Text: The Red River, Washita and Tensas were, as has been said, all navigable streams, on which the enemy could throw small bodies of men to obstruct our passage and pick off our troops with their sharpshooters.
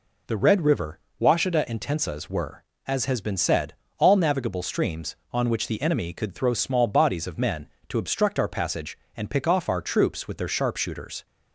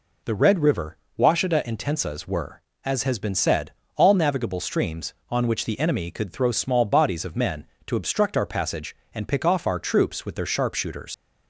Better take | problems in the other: first | leaves "sharpshooters" unfinished; at 11.1 s; 90 ms

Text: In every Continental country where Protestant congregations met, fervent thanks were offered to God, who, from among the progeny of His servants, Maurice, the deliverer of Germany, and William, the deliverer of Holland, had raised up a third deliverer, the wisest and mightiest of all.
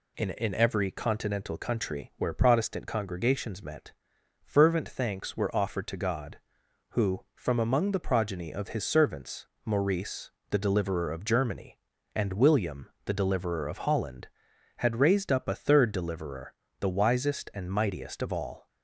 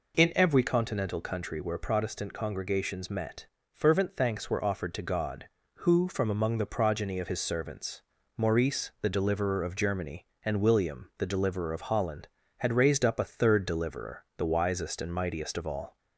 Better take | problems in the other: second | says "In" twice; at 0.3 s

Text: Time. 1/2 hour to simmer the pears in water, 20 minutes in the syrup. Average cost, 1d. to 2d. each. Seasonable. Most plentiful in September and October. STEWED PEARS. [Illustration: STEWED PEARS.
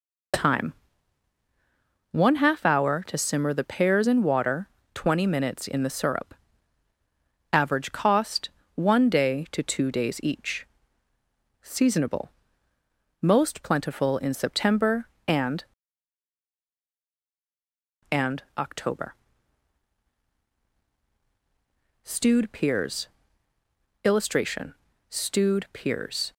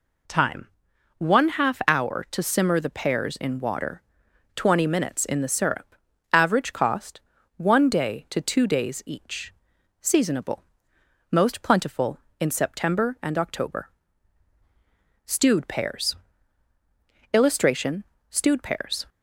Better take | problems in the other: second | says "and" twice; at 18.0 s

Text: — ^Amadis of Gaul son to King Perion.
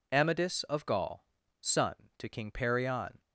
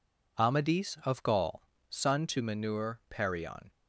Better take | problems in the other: first | pauses between "Gaul" and "son"; slight; at 1.6 s; 0.26 s long; slight in the first // says "Manur" for "King"; at 2.4 s

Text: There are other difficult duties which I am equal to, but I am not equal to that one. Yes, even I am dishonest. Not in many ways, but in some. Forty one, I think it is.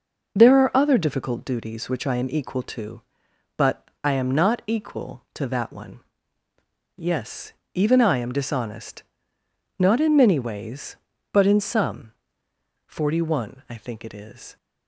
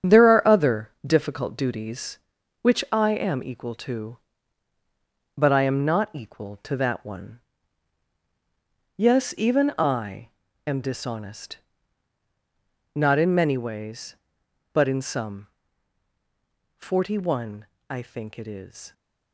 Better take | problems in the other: first | gets quieter; throughout; 7 dB // pauses between "I" and "am"; at 10.2 s; 0.38 s long

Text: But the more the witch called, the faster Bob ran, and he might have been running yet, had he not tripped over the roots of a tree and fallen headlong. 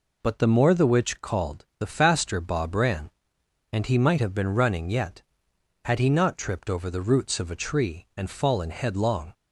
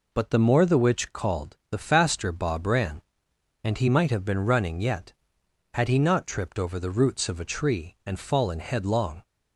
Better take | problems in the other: neither | none

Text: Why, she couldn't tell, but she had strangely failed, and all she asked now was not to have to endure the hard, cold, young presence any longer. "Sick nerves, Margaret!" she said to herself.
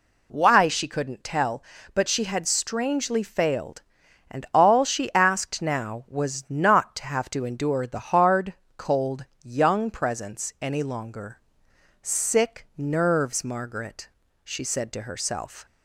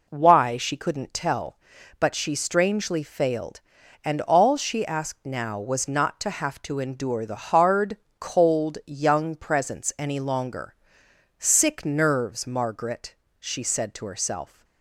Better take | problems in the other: first | skips "had"; at 2.3 s

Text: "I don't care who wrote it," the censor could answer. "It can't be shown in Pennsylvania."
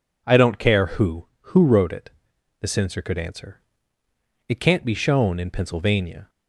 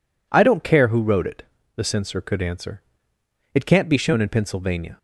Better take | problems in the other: second | says "who" twice; at 1.3 s

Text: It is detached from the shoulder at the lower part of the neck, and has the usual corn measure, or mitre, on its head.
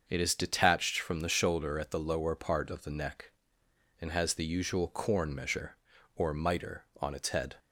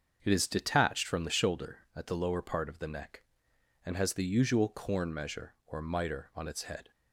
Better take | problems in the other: neither | starts louder than the rest; the same in both

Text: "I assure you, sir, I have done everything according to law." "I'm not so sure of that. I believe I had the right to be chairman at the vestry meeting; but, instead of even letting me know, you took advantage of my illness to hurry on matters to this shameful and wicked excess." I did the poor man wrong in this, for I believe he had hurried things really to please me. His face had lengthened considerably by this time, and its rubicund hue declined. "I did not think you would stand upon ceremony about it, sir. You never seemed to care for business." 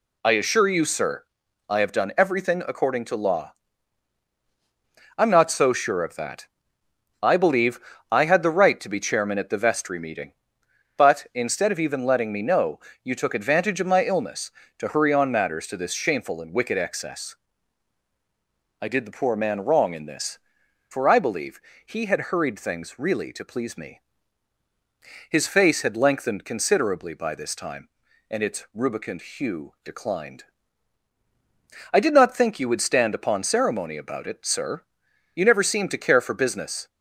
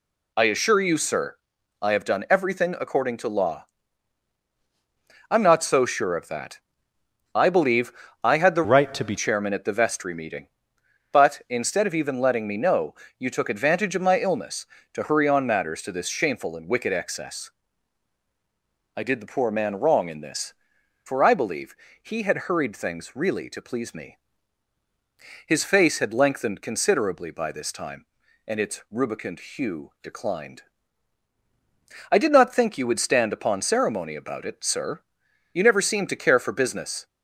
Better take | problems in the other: first | pauses between "believe" and "I"; slight; at 7.9 s; 0.30 s long; slight in the first // changes voice from "right" to "be"; from 8.6 to 9.1 s; 0.5 s long // pauses between "believe" and "he"; slight; at 21.7 s; 0.26 s long; slight in the first

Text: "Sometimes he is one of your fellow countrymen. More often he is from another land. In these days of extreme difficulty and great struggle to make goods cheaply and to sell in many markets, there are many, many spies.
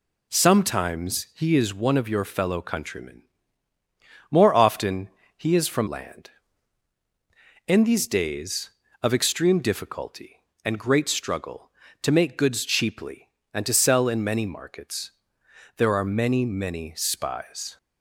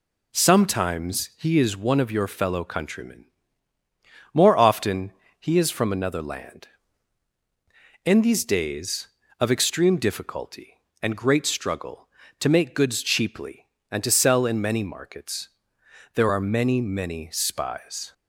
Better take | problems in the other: second | pauses between "often" and "he"; slight; at 5.0 s; 0.28 s long; slight in the second // skips "another"; at 5.8 s

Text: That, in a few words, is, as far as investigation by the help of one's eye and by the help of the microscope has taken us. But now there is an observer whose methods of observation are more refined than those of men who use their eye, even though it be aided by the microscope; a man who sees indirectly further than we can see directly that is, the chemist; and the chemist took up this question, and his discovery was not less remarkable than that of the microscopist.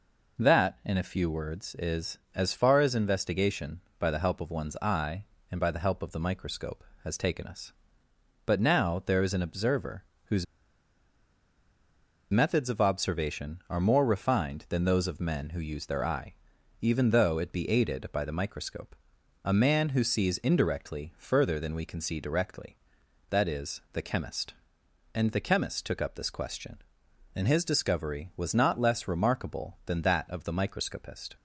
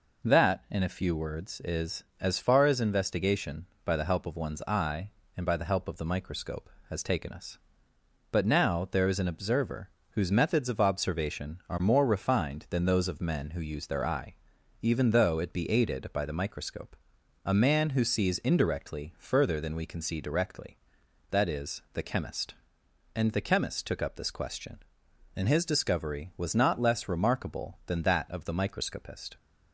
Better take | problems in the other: second | pauses between "observer" and "whose"; slight; at 10.0 s; 0.22 s long; slight in the second // pauses between "whose" and "methods"; strong; at 10.4 s; 1.8 s long

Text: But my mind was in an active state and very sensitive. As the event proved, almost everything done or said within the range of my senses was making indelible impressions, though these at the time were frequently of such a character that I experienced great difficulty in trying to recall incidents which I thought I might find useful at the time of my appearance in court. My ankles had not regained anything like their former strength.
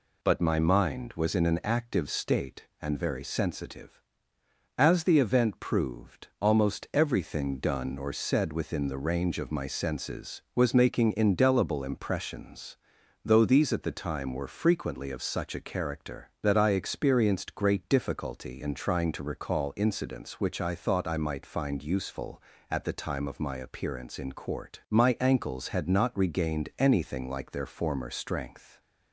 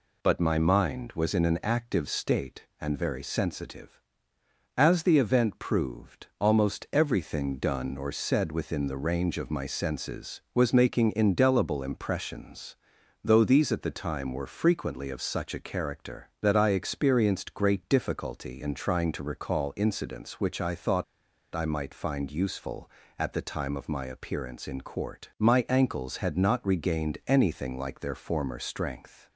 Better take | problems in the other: first | pauses between "thought" and "I"; noticeable; at 21.0 s; 0.50 s long

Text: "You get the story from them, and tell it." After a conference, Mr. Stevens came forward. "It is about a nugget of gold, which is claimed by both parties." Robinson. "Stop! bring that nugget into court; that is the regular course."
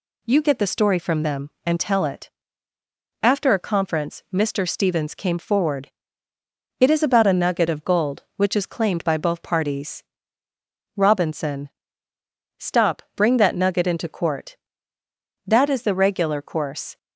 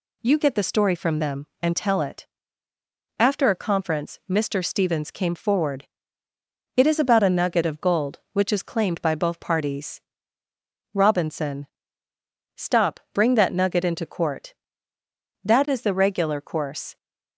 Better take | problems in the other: neither | none

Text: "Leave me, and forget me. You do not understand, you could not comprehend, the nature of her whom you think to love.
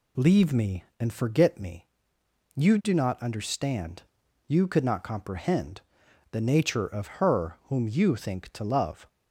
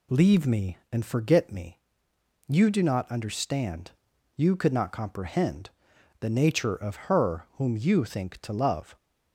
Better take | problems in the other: neither | none

